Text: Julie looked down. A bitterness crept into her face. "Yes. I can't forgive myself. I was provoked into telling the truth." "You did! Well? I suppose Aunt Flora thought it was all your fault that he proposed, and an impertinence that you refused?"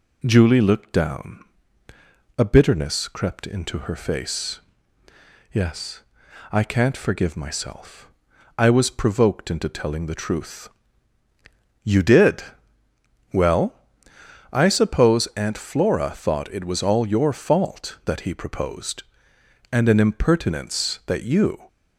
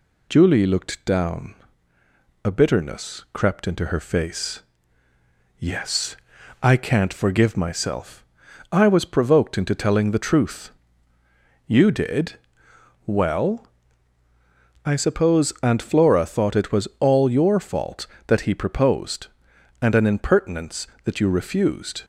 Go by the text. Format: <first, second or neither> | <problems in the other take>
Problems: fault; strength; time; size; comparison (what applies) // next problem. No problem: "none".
second | stops before "refused"; at 21.6 s